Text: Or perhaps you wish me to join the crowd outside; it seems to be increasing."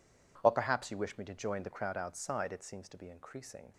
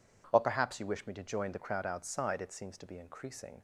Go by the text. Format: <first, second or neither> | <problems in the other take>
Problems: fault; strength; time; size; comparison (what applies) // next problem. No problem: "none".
second | gets quieter; strong; throughout; 17.5 dB